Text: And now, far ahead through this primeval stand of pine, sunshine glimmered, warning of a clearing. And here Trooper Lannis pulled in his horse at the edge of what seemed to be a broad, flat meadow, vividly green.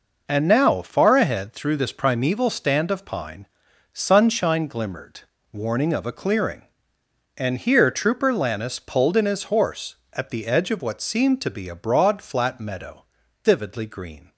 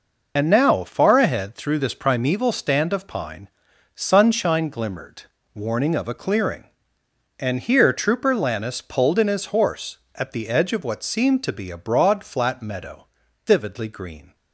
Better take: first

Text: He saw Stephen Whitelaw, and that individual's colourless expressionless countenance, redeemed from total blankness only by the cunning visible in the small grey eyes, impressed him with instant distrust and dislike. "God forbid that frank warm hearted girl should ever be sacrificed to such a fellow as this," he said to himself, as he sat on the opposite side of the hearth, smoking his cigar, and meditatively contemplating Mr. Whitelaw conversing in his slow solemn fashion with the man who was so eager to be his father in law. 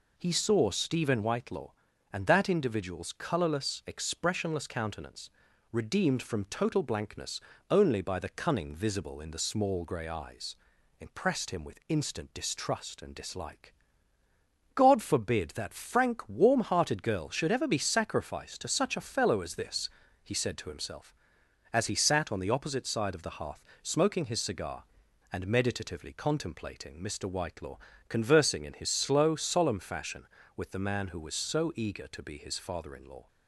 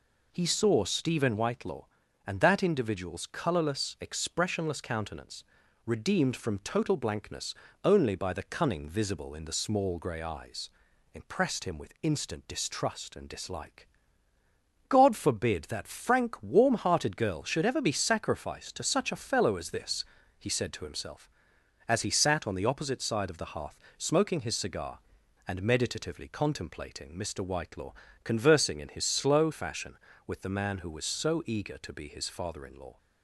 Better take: first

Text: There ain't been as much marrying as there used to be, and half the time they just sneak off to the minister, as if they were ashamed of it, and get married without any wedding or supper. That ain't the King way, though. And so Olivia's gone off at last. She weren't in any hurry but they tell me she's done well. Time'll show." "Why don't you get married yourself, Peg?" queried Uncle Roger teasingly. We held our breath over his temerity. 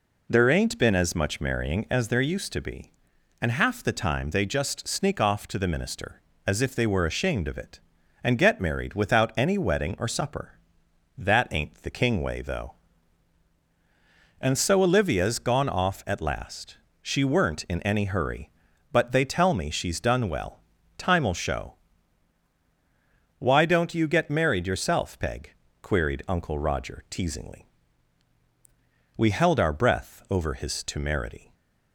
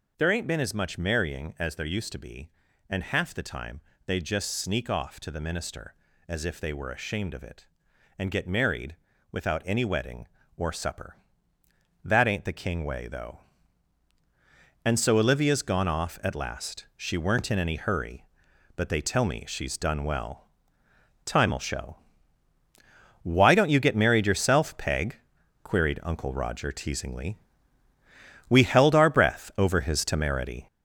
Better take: first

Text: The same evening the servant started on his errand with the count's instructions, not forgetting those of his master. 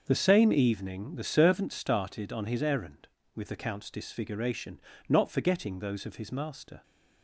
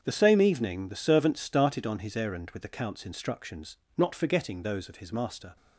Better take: second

